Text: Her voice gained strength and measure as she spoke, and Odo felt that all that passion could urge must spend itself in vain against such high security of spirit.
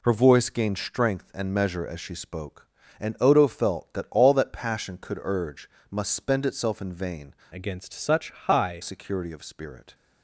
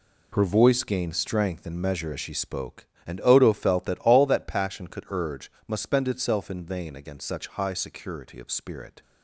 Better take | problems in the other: second | pauses between "urge" and "must"; slight; at 5.6 s; 0.22 s long; slight in the second // changes voice from "against" to "high"; from 7.5 to 8.8 s; 1.3 s long

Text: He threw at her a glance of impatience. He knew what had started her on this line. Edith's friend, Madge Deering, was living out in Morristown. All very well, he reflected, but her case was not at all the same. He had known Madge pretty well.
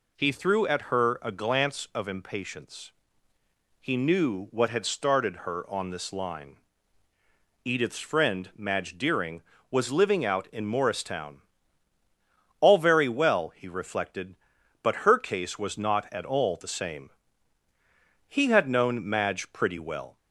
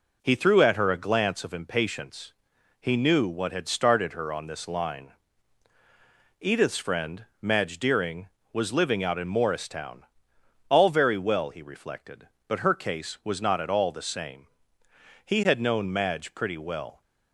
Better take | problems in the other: neither | none

